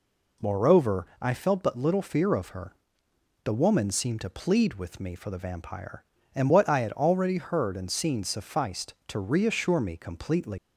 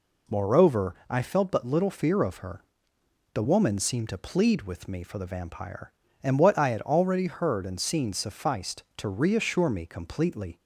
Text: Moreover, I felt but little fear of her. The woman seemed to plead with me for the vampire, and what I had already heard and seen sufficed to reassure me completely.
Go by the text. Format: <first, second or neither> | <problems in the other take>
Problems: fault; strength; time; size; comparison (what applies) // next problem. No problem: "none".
second | leaves "completely" unfinished; at 10.5 s; 105 ms